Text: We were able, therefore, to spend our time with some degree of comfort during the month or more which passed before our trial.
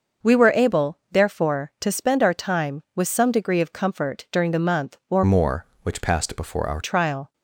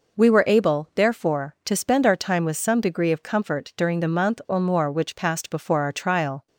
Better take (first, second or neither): second